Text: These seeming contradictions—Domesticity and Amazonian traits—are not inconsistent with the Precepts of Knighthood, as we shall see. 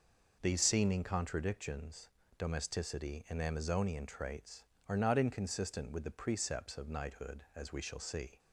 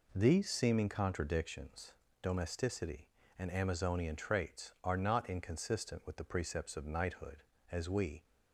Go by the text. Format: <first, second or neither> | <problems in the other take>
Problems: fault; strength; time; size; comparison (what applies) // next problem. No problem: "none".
first | stops before "shall see"; at 8.2 s